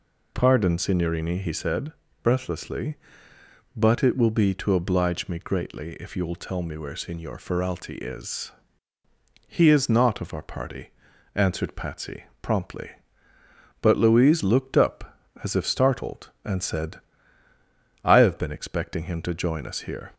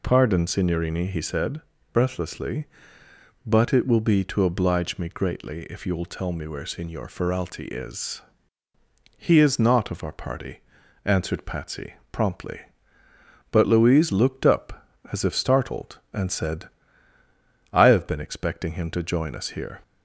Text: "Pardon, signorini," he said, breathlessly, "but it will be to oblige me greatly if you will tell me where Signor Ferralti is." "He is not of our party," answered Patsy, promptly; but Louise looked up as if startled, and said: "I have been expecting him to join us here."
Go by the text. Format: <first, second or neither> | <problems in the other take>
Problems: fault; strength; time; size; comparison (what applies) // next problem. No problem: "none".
neither | none